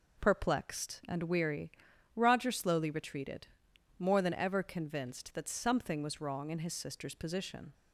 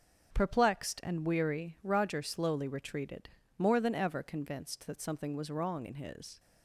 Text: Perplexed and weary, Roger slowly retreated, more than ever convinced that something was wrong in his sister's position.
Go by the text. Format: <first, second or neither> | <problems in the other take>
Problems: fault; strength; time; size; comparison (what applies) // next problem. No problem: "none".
first | starts louder than the rest; until 1.3 s; 6.5 dB // stops before "sister's position"; at 6.3 s